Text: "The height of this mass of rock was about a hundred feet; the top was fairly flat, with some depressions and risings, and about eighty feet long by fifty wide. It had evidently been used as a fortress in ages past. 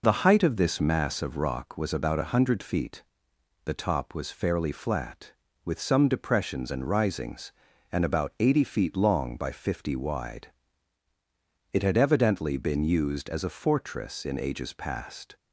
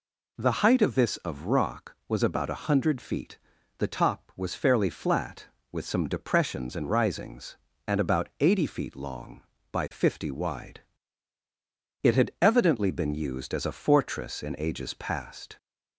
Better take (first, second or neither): first